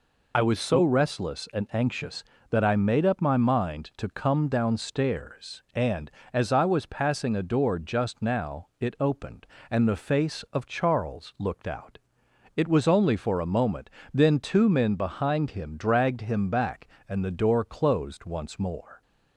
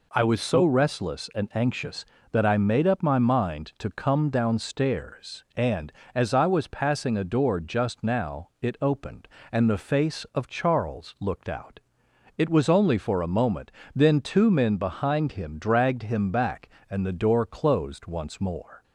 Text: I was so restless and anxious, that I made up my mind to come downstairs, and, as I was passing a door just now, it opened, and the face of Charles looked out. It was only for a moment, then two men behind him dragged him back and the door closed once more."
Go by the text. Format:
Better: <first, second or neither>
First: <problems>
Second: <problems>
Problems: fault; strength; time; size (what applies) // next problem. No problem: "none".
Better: second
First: loses the start of "I"; at 0.3 s; 55 ms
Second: none